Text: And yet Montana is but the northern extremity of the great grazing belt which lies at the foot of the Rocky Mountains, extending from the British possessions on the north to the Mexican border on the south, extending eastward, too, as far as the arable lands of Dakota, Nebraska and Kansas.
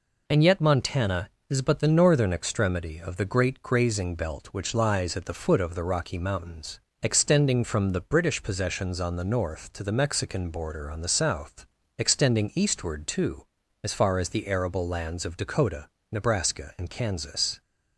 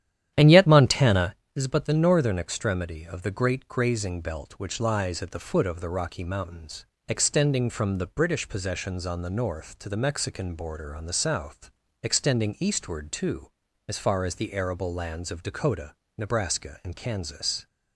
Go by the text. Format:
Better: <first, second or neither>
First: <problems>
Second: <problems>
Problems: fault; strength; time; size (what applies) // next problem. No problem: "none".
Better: first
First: none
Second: starts louder than the rest; strong; until 1.3 s; 11 dB